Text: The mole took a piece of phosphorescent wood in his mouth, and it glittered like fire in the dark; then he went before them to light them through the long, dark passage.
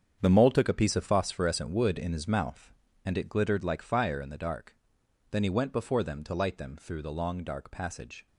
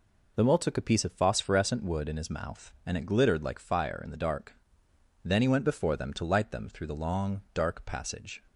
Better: second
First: gets quieter; strong; throughout; 11.5 dB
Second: none

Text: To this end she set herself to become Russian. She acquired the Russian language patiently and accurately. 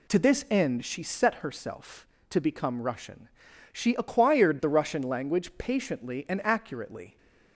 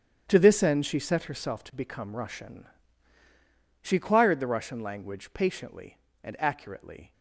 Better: first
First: none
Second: gets quieter; strong; throughout; 12.5 dB

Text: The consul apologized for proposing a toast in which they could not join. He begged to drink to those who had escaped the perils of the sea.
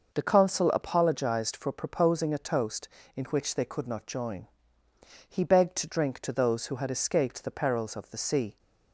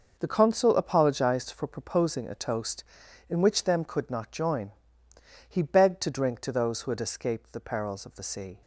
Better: first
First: none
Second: says "them" for "they"; at 3.6 s

